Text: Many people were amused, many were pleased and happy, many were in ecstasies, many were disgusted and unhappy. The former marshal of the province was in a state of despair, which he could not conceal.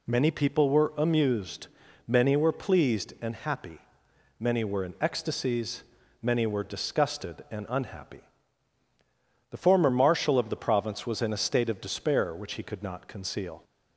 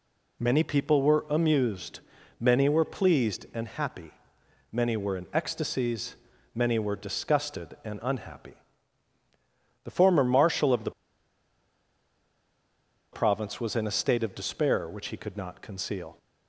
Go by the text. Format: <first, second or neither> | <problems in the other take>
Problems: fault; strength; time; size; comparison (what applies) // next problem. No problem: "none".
first | pauses between "the" and "province"; strong; at 10.9 s; 2.2 s long